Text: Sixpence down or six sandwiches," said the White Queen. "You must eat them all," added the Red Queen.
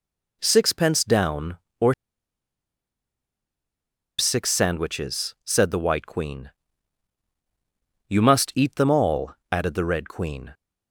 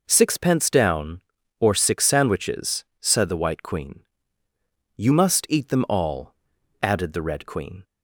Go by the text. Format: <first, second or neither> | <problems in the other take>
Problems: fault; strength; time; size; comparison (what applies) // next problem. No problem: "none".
second | pauses between "or" and "six"; strong; at 1.9 s; 2.2 s long